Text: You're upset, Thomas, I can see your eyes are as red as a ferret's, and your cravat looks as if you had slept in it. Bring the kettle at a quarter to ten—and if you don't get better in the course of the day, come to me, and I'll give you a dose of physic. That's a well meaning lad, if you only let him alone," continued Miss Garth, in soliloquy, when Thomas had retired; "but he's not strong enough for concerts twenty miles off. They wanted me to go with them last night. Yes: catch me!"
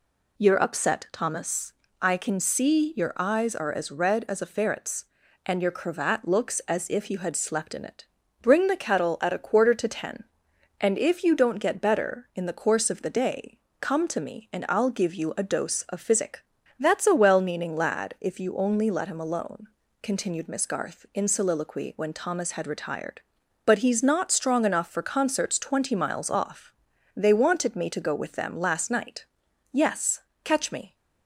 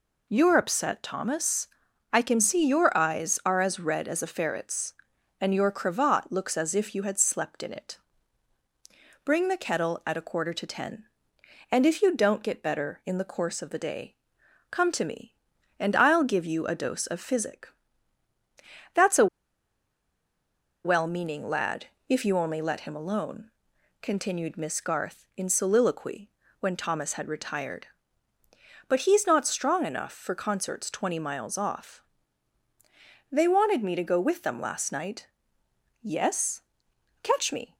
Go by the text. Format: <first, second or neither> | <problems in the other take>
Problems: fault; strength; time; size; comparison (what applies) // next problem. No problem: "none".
first | pauses between "a" and "well"; strong; at 19.2 s; 1.5 s long